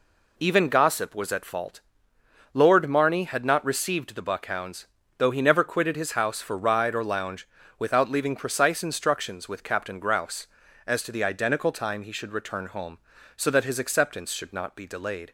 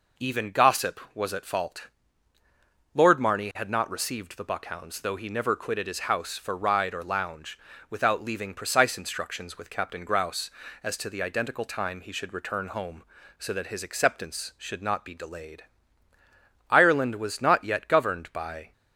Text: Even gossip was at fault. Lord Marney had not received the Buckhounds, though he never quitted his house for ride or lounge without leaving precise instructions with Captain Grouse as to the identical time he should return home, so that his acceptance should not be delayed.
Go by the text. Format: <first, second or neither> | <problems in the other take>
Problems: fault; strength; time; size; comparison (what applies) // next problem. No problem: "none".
first | pauses between "lounge" and "without"; slight; at 7.5 s; 0.32 s long; slight in the first // goes on to say "Ireland was not yet governed by"; strong; from 16.6 s on; 2.0 s long